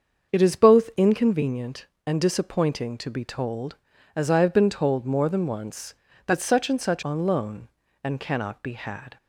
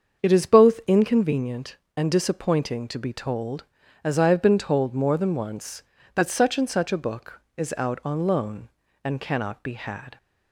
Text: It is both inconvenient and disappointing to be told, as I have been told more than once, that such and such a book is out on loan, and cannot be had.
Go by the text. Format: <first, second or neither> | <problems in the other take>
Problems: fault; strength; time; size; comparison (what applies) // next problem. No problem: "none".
second | starts louder than the rest; until 1.3 s; 7 dB; also in the second // skips "a book is out"; at 7.0 s